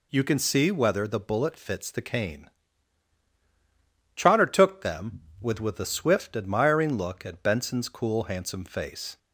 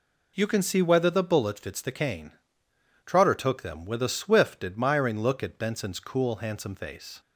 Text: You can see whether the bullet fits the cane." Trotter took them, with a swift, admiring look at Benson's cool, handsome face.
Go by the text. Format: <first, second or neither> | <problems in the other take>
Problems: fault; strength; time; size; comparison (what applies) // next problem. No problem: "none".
second | says "with" twice; at 5.5 s